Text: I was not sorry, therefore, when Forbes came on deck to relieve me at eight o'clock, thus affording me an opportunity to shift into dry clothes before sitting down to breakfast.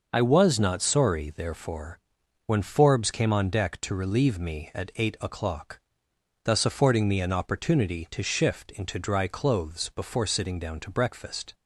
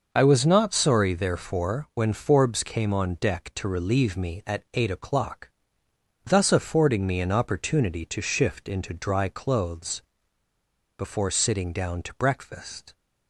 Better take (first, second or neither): first